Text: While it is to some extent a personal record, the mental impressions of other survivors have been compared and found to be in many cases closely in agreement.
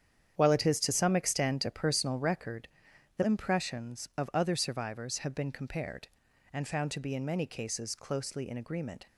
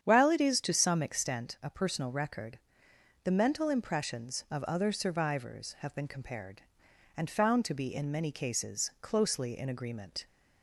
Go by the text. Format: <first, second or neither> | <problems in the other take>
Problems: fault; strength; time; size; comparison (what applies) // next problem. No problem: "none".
second | starts louder than the rest; strong; until 1.3 s; 9 dB; strong in the second // skips "mental"; at 3.2 s